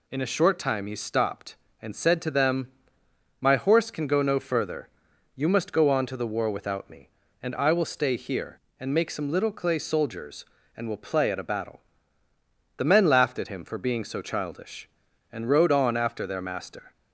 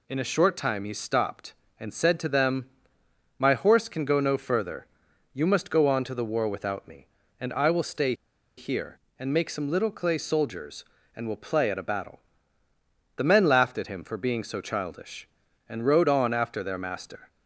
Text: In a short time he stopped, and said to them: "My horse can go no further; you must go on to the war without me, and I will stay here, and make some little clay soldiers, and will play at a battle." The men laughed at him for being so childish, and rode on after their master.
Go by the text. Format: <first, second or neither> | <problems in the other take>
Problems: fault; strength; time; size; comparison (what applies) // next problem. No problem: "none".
first | pauses between "stay" and "here"; at 8.1 s; 0.44 s long